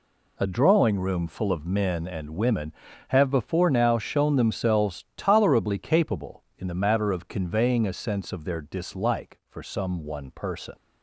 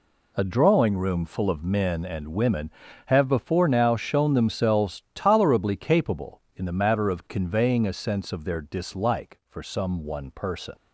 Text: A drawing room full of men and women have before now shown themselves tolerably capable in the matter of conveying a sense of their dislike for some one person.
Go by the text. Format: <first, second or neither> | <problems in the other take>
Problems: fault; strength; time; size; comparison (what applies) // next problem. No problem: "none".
neither | none